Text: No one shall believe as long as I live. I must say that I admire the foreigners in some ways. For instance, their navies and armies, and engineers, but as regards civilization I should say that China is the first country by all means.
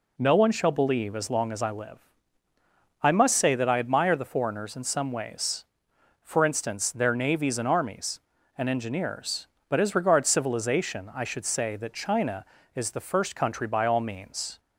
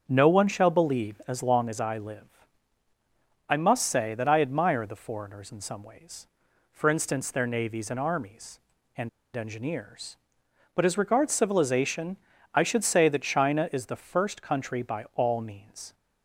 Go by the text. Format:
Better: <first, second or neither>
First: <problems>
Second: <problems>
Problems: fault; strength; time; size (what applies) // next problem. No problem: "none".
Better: first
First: none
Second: starts louder than the rest; until 1.0 s; 7 dB // pauses between "and" and "engineers"; slight; at 9.0 s; 0.26 s long // pauses between "civilization" and "I"; at 12.1 s; 0.38 s long